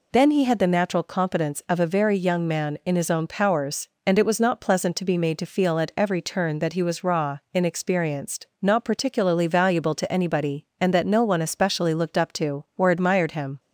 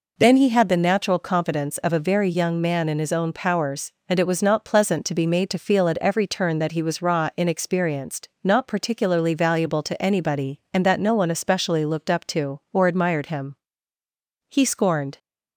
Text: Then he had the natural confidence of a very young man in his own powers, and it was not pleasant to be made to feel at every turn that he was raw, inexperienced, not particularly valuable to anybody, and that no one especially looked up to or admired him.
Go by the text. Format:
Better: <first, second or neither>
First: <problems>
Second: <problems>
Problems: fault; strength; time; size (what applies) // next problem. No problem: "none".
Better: first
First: none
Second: goes on to say "He scorned"; noticeable; from 14.4 s on; 0.70 s long